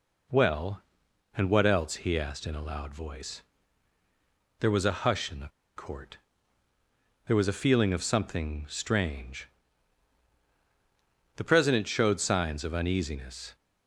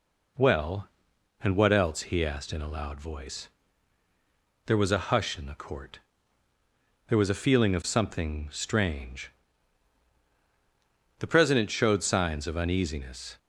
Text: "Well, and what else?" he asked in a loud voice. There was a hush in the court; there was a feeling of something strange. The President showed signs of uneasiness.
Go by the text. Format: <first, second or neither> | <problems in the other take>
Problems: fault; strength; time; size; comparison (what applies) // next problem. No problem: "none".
second | pauses between "the" and "court"; slight; at 5.4 s; 0.27 s long